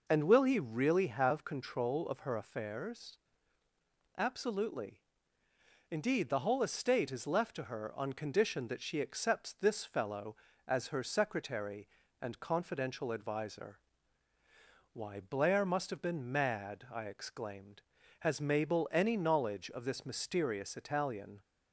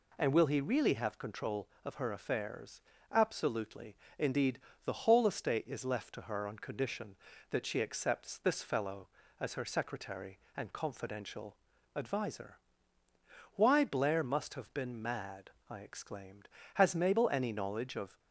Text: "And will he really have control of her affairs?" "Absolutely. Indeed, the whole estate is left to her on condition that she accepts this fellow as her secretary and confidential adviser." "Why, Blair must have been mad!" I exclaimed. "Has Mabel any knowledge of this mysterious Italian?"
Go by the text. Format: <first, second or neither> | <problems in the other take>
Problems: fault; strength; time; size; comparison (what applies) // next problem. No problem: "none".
first | pauses between "confidential" and "adviser"; at 11.5 s; 0.40 s long // stops before "this mysterious Italian"; at 18.1 s